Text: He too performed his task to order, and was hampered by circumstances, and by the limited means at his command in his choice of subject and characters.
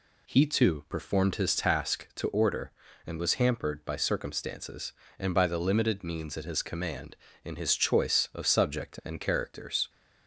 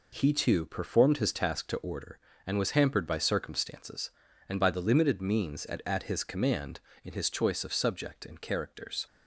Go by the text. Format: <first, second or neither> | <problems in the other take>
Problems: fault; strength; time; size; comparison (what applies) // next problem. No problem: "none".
first | says "at" twice; at 5.8 s